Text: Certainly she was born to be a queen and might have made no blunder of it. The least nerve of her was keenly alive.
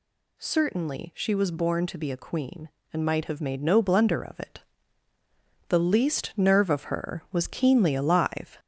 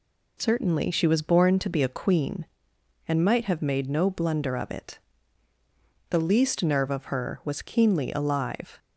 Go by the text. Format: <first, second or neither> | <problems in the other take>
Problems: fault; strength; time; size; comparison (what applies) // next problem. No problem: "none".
second | gets louder; slight; throughout; 3 dB